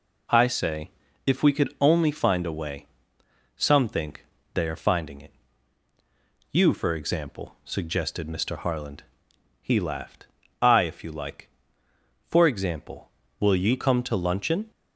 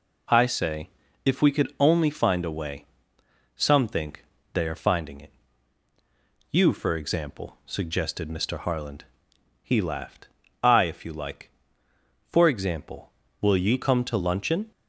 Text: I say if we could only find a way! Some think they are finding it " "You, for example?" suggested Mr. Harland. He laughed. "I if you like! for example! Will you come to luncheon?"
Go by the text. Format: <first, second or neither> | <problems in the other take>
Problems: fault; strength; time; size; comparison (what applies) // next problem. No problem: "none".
neither | pauses between "say" and "if"; the same in both // pauses between "think" and "they"; slight; the same in both